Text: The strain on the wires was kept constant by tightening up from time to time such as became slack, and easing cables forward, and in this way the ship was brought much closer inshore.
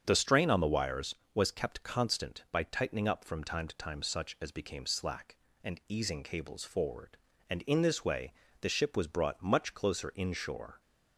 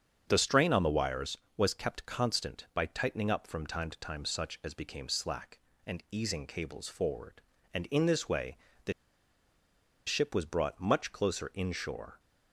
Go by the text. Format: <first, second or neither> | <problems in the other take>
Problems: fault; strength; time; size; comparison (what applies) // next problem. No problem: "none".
first | starts louder than the rest; strong; until 1.3 s; 7.5 dB; strong in the first // pauses between "way" and "the"; slight; at 8.5 s; 0.26 s long; slight in the first // pauses between "the" and "ship"; at 8.9 s; 1.1 s long